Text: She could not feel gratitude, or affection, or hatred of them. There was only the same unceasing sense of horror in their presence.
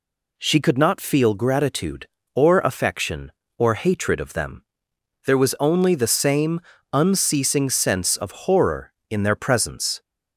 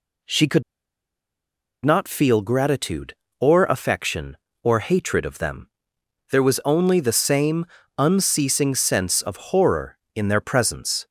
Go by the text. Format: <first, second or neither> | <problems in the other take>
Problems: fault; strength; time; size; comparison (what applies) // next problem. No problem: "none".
first | pauses between "could" and "not"; at 0.6 s; 1.2 s long // pauses between "same" and "unceasing"; slight; at 7.6 s; 0.34 s long; slight in the first